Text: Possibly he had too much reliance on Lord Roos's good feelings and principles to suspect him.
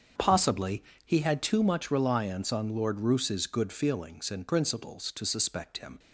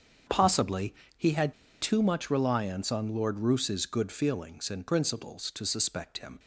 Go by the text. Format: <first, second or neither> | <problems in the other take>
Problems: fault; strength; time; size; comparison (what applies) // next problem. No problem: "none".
first | starts louder than the rest; strong; until 1.5 s; 7 dB; strong in the first // pauses between "Possibly" and "he"; slight; at 0.9 s; 0.22 s long; slight in the first // pauses between "had" and "too"; slight; at 1.5 s; 0.27 s long